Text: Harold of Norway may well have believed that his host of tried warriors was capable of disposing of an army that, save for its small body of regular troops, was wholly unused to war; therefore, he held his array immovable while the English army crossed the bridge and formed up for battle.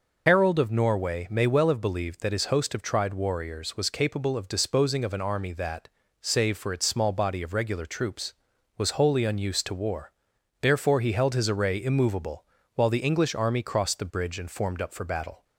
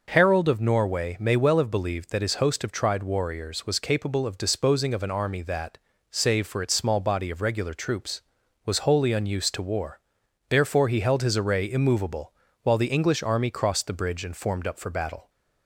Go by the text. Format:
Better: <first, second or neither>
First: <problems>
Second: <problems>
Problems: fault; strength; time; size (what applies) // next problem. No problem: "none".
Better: second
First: loses the start of "Harold"; at 0.2 s; 75 ms // pauses between "immovable" and "while"; slight; at 12.4 s; 0.32 s long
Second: pauses between "immovable" and "while"; slight; at 12.3 s; 0.32 s long